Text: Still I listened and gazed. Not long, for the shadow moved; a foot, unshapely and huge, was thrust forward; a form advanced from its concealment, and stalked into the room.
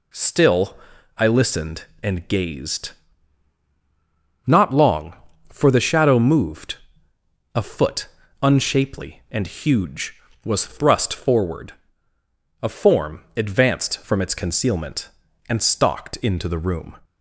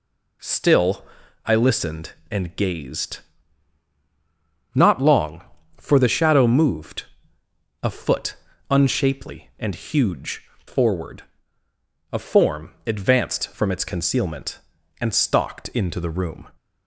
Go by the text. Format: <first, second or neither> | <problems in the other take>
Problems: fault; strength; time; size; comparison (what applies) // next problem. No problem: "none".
first | pauses between "Still" and "I"; at 1.0 s; 0.40 s long; also in the first // skips "was thrust"; at 10.5 s // pauses between "form" and "advanced"; slight; at 12.7 s; 0.16 s long; slight in the first